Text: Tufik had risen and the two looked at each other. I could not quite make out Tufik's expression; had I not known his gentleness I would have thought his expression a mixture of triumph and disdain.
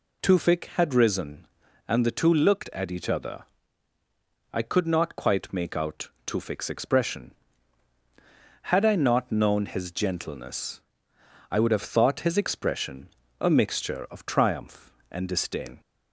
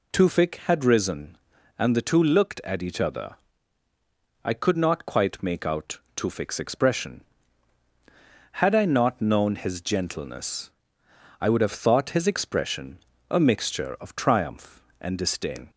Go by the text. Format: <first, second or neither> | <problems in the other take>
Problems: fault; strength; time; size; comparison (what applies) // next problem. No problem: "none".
neither | pauses between "out" and "Tufik's"; slight; the same in both // pauses between "gentleness" and "I"; noticeable; the same in both // pauses between "expression" and "a"; slight; the same in both